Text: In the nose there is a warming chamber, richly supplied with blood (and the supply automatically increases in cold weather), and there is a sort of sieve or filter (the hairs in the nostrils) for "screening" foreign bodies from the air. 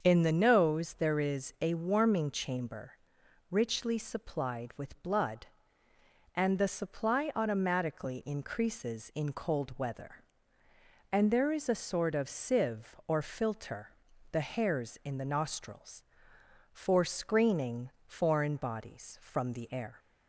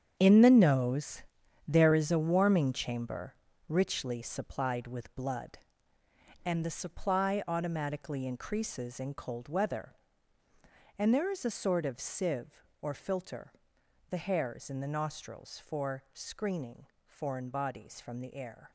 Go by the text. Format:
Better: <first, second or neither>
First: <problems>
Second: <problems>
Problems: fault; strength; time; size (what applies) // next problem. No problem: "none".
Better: first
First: starts louder than the rest; until 1.0 s; 7 dB // pauses between "screening" and "foreign"; slight; at 17.9 s; 0.16 s long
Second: gets quieter; strong; throughout; 11.5 dB // starts louder than the rest; strong; until 1.2 s; 8.5 dB // pauses between "nose" and "there"; noticeable; at 1.2 s; 0.46 s long // pauses between "screening" and "foreign"; slight; at 16.8 s; 0.18 s long